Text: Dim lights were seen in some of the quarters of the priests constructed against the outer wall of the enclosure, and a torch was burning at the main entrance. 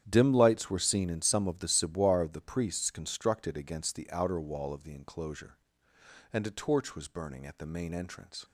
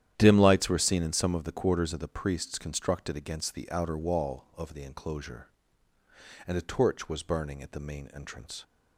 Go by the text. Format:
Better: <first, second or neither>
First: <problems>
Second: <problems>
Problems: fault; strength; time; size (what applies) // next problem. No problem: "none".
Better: second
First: starts louder than the rest; strong; until 1.0 s; 10 dB // says "ciboire" for "quarters"; at 1.6 s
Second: starts louder than the rest; strong; until 1.1 s; 10.5 dB